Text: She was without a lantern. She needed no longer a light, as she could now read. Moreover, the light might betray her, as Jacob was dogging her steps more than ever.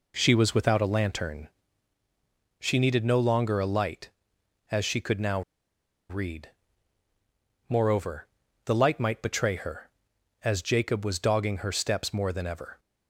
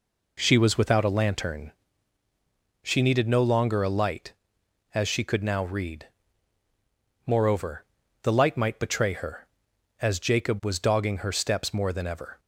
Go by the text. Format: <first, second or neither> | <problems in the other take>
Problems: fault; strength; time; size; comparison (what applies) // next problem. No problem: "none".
second | pauses between "now" and "read"; noticeable; at 5.4 s; 0.68 s long